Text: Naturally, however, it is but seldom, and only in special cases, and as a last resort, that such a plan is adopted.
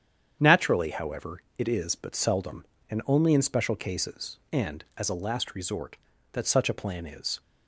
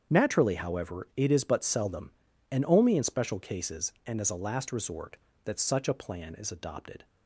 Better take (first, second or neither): second